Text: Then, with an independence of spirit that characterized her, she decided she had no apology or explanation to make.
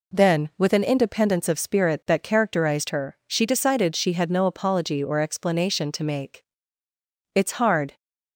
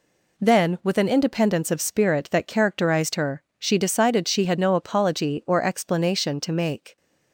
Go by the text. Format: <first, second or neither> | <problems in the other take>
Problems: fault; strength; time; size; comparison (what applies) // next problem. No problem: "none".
second | goes on to say "It's hard"; noticeable; from 7.3 s on; 0.62 s long